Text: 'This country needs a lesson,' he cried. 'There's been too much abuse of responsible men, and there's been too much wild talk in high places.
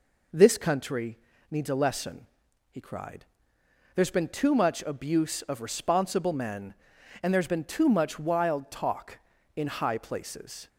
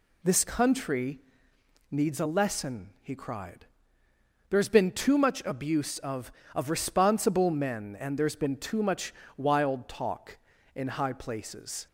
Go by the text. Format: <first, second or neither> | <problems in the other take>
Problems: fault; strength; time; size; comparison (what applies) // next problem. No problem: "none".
first | pauses between "country" and "needs"; noticeable; at 1.1 s; 0.72 s long; slight in the first // says "of" twice; at 6.5 s // pauses between "much" and "wild"; slight; at 9.1 s; 0.24 s long